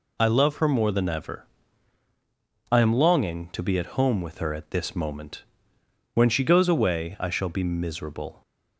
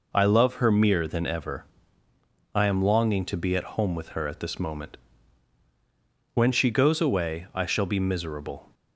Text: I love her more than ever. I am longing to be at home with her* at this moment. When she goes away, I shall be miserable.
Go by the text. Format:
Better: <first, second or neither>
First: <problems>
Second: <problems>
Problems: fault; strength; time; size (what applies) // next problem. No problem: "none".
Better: first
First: none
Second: says "mere" for "more"; at 0.6 s